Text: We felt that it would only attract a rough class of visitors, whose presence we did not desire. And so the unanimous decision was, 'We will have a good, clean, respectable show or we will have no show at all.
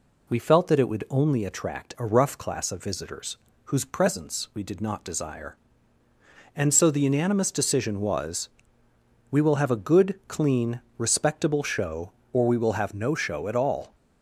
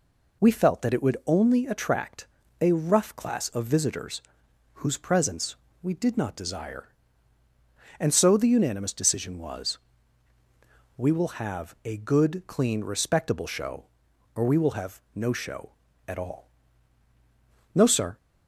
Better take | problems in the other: first | pauses between "attract" and "a"; slight; at 2.2 s; 0.34 s long // pauses between "presence" and "we"; slight; at 5.5 s; 0.28 s long // goes on to say "No sir"; slight; from 17.7 s on; 0.44 s long

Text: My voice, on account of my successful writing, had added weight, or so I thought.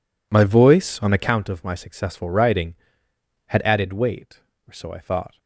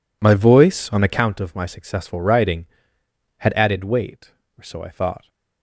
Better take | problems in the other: neither | none

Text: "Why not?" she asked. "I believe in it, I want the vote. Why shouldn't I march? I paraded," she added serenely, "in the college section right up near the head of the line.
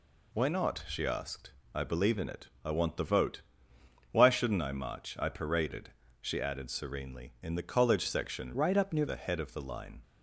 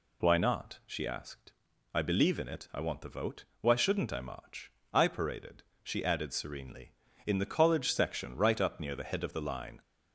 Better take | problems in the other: second | changes voice from "right" to "near"; from 8.5 to 9.0 s; 0.5 s long

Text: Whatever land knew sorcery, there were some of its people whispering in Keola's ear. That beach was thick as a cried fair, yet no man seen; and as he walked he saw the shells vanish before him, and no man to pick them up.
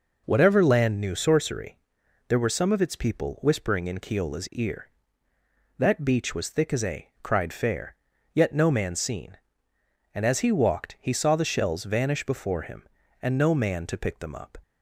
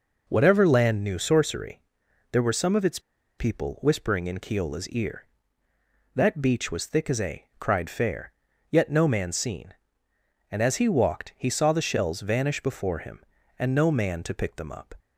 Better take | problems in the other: first | pauses between "its" and "people"; at 2.9 s; 0.39 s long // pauses between "a" and "cried"; slight; at 7.4 s; 0.16 s long; slight in the first

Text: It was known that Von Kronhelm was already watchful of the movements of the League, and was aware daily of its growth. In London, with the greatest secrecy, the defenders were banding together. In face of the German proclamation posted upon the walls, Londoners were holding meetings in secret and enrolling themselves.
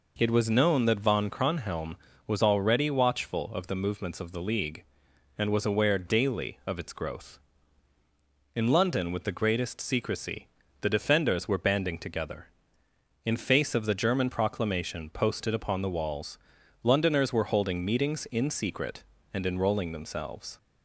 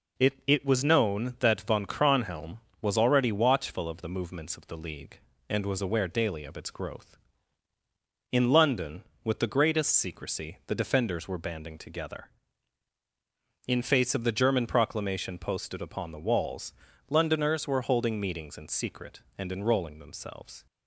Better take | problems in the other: first | says "It" twice; at 0.4 s

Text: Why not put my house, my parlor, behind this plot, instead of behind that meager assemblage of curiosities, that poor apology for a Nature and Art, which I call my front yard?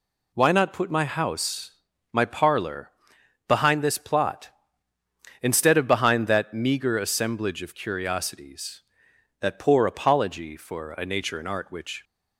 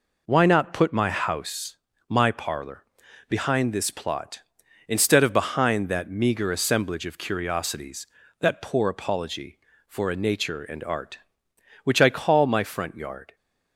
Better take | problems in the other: second | stops before "I call my front yard"; at 12.0 s

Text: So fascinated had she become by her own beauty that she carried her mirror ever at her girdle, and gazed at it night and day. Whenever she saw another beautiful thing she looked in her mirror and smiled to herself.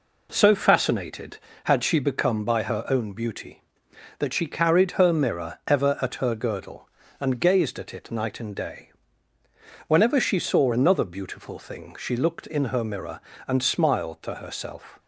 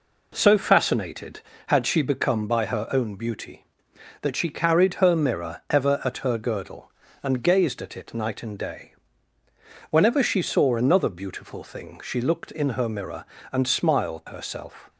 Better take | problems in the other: first | skips "to"; at 14.2 s

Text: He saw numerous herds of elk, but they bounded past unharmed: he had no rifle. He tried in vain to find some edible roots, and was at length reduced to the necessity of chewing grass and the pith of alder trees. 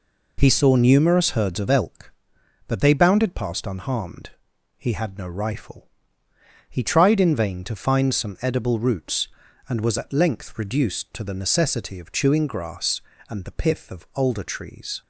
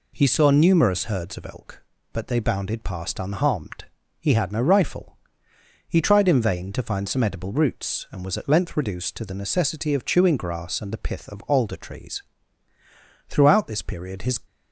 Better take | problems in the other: first | goes on to say "Throughout this period his"; noticeable; from 13.3 s on; 1.0 s long

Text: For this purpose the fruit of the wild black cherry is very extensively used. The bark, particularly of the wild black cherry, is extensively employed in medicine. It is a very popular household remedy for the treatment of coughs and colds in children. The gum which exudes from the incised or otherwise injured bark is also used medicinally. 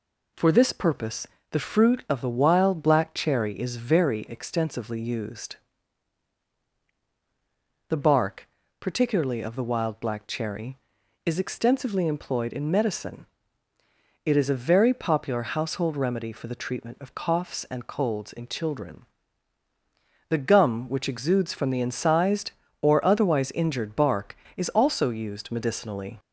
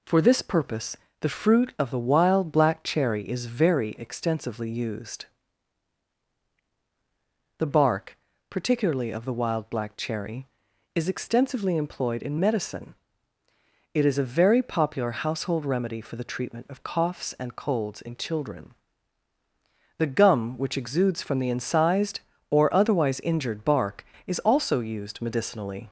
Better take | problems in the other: neither | pauses between "purpose" and "the"; slight; the same in both

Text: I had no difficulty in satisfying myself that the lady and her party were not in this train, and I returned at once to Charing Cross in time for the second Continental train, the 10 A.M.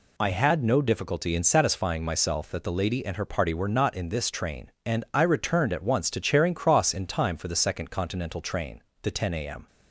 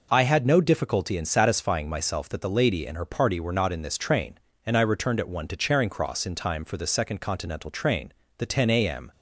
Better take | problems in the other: first | says "one" for "once"; at 5.2 s

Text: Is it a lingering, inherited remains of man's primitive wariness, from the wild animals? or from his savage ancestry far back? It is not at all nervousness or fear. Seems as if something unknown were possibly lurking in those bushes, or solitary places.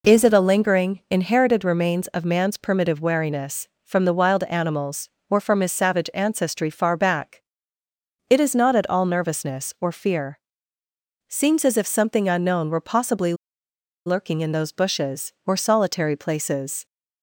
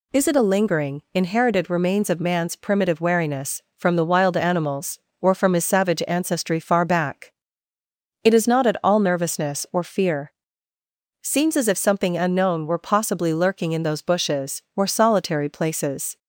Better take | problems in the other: second | pauses between "possibly" and "lurking"; noticeable; at 13.3 s; 0.72 s long

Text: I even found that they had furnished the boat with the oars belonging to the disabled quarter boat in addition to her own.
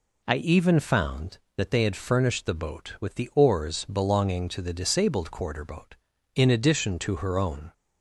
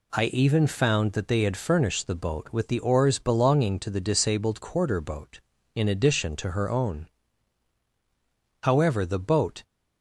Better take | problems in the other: first | goes on to say "However the boat"; noticeable; from 8.6 s on; 1.0 s long

